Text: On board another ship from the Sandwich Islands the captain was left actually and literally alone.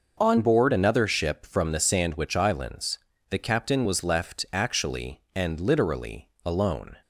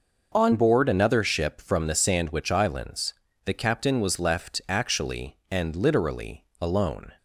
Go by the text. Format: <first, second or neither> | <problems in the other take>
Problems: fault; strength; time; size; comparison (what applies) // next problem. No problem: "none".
neither | pauses between "Islands" and "the"; slight; the same in both // pauses between "literally" and "alone"; slight; the same in both